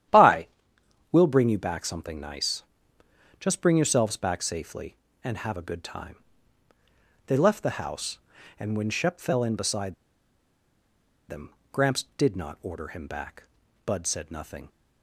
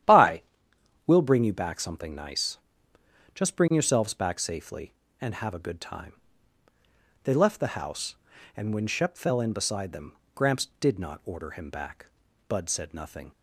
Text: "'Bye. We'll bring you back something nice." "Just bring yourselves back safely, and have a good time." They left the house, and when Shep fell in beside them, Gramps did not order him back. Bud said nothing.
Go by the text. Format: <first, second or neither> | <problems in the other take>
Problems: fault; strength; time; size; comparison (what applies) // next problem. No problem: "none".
second | starts louder than the rest; strong; until 1.7 s; 11 dB; strong in the second // pauses between "beside" and "them"; strong; at 9.9 s; 1.3 s long